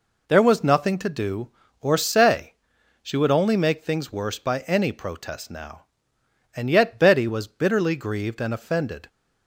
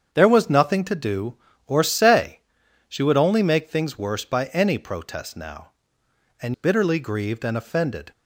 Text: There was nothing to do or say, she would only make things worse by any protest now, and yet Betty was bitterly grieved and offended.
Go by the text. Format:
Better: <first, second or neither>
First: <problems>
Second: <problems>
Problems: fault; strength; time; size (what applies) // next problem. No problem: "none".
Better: first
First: none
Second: starts louder than the rest; strong; until 1.1 s; 7.5 dB // skips "yet Betty was"; at 6.5 s